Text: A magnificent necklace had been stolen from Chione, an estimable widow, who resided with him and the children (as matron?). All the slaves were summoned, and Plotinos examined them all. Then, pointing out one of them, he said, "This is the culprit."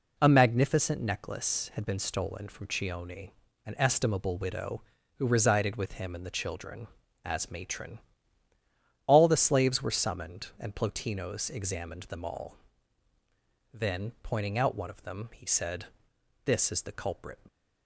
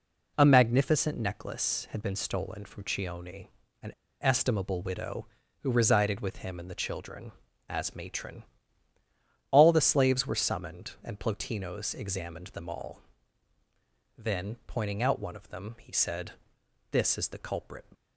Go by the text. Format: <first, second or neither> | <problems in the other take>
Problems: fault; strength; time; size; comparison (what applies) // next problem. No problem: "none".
first | pauses between "an" and "estimable"; slight; at 3.9 s; 0.29 s long